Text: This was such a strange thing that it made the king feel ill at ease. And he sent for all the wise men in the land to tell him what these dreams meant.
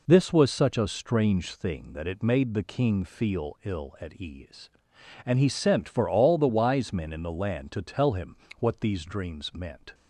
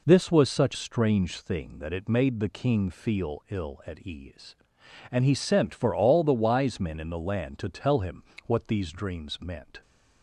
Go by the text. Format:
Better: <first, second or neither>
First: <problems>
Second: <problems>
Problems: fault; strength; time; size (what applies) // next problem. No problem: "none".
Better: first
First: pauses between "him" and "what"; slight; at 8.3 s; 0.24 s long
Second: skips "a"; at 0.7 s // pauses between "him" and "what"; slight; at 8.2 s; 0.24 s long